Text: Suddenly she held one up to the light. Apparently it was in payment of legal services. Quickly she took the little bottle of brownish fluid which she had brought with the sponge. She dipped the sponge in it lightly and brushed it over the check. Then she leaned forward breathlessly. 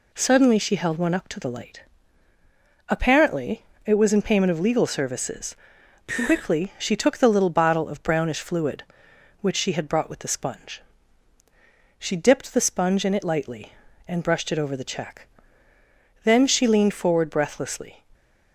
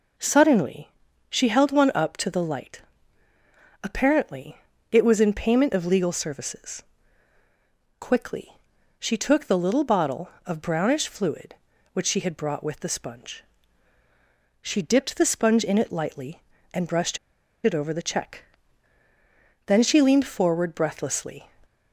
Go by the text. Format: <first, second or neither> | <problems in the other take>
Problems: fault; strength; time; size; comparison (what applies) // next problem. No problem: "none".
first | pauses between "Suddenly" and "she"; at 0.8 s; 0.40 s long // pauses between "Apparently" and "it"; slight; at 4.5 s; 0.34 s long; slight in the first // pauses between "Quickly" and "she"; noticeable; at 8.5 s; 0.46 s long // pauses between "brushed" and "it"; noticeable; at 17.1 s; 0.46 s long